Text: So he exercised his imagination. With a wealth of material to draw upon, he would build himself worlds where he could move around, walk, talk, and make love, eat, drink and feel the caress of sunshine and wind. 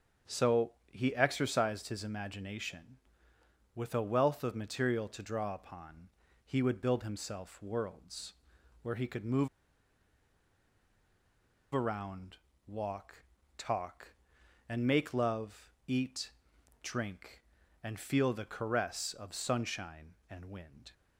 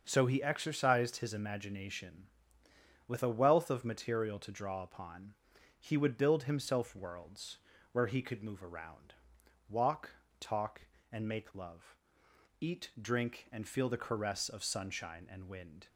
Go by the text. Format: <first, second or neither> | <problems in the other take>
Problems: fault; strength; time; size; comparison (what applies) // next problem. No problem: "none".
second | starts louder than the rest; strong; until 1.4 s; 7 dB; also in the second // pauses between "So" and "he"; slight; at 0.7 s; 0.20 s long // pauses between "worlds" and "where"; noticeable; at 8.3 s; 0.50 s long; slight in the second // pauses between "move" and "around"; strong; at 9.4 s; 2.2 s long